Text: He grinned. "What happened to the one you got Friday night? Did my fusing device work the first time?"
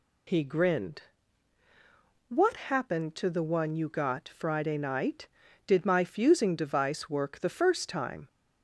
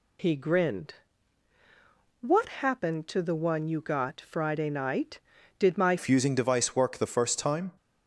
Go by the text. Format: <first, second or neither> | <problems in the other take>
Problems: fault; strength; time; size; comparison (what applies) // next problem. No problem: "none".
first | changes voice at "fusing"; from 5.9 s on; 1.8 s long